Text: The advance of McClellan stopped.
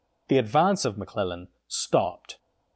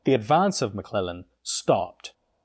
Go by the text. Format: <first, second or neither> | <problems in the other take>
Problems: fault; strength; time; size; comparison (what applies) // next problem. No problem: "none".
neither | pauses between "McClellan" and "stopped"; slight; the same in both